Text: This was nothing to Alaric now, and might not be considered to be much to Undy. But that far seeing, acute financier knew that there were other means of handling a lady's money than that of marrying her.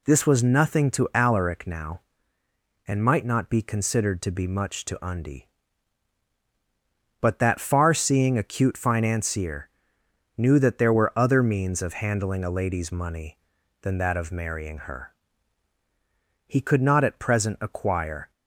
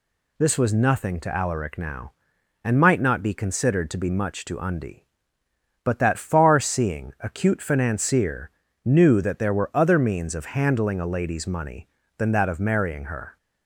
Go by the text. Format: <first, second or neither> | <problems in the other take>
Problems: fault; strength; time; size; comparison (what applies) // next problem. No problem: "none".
second | pauses between "financier" and "knew"; noticeable; at 9.6 s; 0.68 s long; slight in the second // goes on to say "He could not at present acquire"; strong; from 16.4 s on; 1.8 s long